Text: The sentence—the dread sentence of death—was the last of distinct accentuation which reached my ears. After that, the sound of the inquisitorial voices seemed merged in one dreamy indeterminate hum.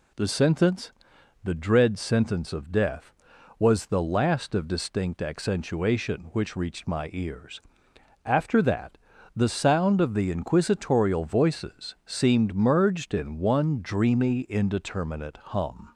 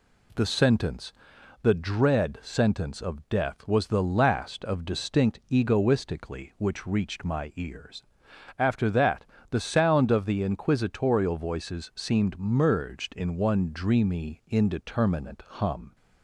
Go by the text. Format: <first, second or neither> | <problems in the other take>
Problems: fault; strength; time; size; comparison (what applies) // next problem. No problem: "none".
first | says "egoistically" for "accentuation"; at 5.5 s